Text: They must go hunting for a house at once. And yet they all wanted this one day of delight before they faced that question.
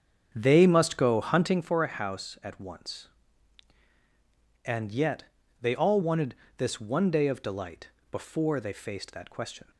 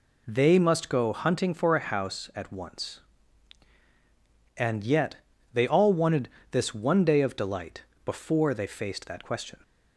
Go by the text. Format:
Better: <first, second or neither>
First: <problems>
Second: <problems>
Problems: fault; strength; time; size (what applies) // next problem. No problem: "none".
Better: second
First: starts louder than the rest; strong; until 1.7 s; 7.5 dB // pauses between "yet" and "they"; at 5.2 s; 0.38 s long // pauses between "wanted" and "this"; slight; at 6.3 s; 0.22 s long // pauses between "delight" and "before"; slight; at 7.8 s; 0.22 s long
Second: pauses between "yet" and "they"; at 5.1 s; 0.38 s long // pauses between "wanted" and "this"; slight; at 6.2 s; 0.22 s long // pauses between "delight" and "before"; slight; at 7.8 s; 0.22 s long